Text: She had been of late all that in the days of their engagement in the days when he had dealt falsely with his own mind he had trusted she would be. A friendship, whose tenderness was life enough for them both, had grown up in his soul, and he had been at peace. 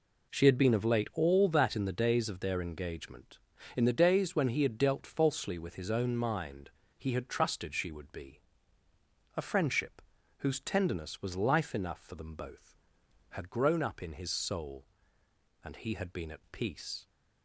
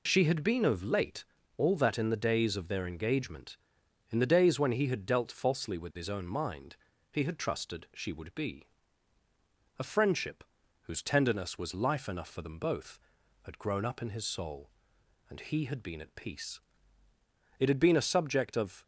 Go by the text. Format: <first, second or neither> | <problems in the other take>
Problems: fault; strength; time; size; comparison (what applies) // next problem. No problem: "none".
first | pauses between "late" and "all"; slight; at 1.2 s; 0.32 s long // pauses between "mind" and "he"; at 6.7 s; 0.38 s long; slight in the first // goes on to say "It had been a subject of"; noticeable; from 17.6 s on; 1.2 s long